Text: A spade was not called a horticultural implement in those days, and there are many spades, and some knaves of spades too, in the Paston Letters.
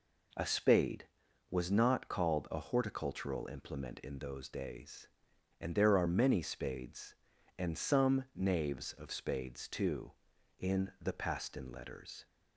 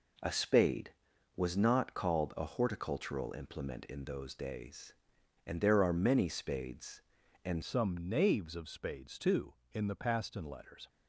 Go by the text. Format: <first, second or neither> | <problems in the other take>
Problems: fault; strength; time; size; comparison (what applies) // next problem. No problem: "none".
first | changes voice at "some"; from 7.6 s on; 3.2 s long